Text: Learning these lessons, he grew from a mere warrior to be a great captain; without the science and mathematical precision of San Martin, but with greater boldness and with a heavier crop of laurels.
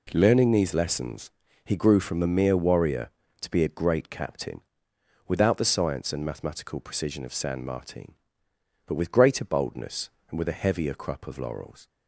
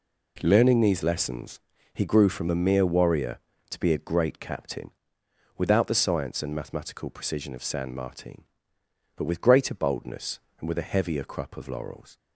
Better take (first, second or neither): neither